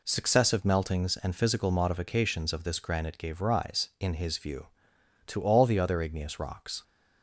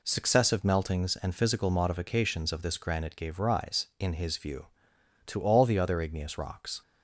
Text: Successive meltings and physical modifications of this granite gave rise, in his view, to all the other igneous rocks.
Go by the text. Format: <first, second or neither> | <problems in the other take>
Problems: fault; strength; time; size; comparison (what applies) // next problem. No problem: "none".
neither | none